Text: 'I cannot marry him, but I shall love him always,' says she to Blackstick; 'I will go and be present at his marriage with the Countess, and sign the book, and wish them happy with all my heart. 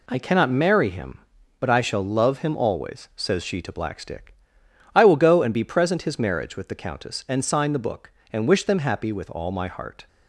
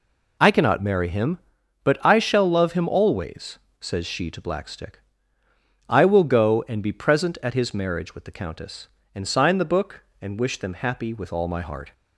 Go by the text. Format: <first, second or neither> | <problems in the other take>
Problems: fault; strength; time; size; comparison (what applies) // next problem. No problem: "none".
second | skips "at"; at 6.0 s